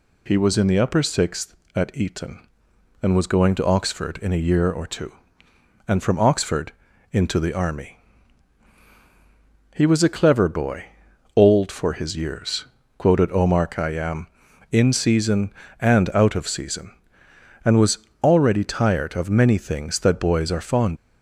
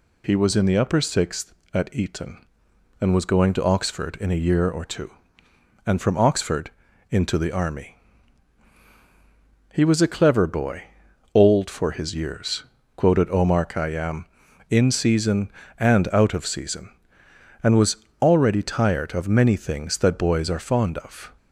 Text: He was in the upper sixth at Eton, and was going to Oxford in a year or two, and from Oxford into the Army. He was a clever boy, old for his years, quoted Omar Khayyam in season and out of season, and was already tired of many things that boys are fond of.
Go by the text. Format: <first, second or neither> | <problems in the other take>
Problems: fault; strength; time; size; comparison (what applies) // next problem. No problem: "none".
second | pauses between "Oxford" and "into"; at 6.7 s; 0.40 s long; also in the second // pauses between "was" and "already"; slight; at 17.9 s; 0.22 s long; slight in the second // stops before "of"; at 20.9 s